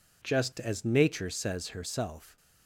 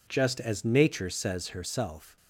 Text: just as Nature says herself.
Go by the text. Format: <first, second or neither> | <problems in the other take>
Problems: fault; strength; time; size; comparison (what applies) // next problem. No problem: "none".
neither | none